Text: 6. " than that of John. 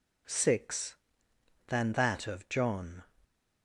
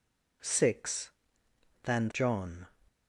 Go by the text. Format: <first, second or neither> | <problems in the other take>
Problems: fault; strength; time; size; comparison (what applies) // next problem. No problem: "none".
first | skips "that of"; at 2.1 s